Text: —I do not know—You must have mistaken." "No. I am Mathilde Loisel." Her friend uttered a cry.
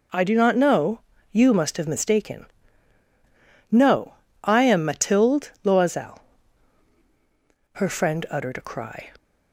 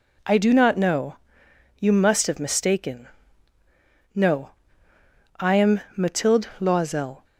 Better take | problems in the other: first | pauses between "am" and "Mathilde"; slight; at 5.7 s; 0.16 s long // stops before "Her friend uttered a cry"; at 7.2 s

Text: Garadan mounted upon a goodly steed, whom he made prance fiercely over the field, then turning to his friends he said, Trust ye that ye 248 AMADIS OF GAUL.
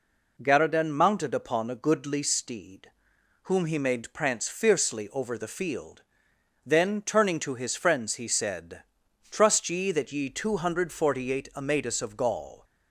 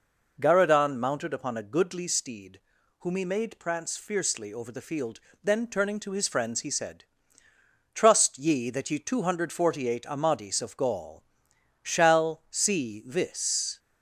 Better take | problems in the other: first | goes on to say "shall see this"; strong; from 11.8 s on; 1.9 s long

